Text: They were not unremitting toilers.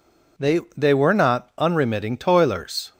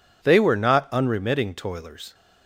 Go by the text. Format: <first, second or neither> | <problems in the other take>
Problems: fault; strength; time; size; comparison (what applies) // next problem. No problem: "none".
second | says "They" twice; at 0.7 s